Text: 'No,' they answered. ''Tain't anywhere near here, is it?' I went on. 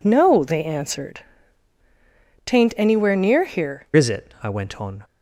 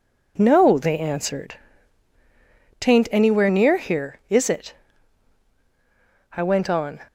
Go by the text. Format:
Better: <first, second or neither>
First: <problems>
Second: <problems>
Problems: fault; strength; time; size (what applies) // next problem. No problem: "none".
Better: second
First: changes voice at "is"; from 3.9 s on; 1.1 s long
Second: none